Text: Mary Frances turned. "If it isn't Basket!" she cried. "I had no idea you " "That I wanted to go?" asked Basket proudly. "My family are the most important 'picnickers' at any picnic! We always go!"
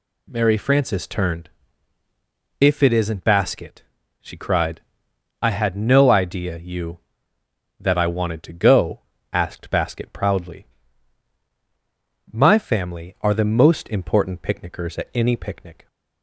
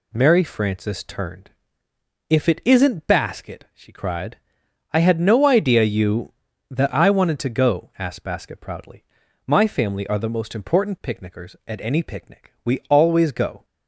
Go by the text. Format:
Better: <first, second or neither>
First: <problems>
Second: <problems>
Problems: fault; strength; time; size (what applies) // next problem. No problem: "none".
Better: second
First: stops before "We always go"; at 15.8 s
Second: none